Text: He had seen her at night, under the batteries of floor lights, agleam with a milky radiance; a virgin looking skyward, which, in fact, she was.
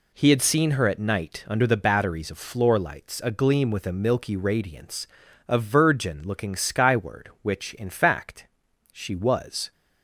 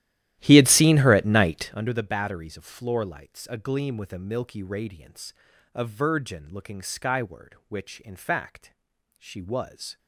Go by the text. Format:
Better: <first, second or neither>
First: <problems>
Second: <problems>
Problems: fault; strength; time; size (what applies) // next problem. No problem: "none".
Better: first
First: none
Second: starts louder than the rest; strong; until 1.9 s; 13.5 dB